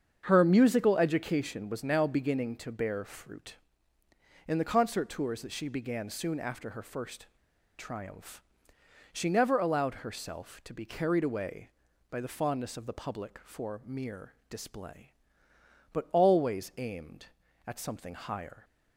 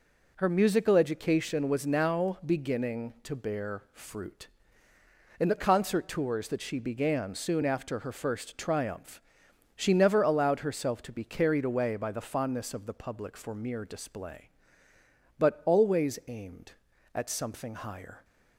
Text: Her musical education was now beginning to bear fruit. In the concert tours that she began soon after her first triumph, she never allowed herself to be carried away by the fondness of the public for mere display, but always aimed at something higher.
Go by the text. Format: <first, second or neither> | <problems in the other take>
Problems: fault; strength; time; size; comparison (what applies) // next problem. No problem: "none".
second | starts louder than the rest; strong; until 1.2 s; 7 dB // pauses between "first" and "triumph"; noticeable; at 7.2 s; 0.51 s long // pauses between "mere" and "display"; slight; at 14.3 s; 0.16 s long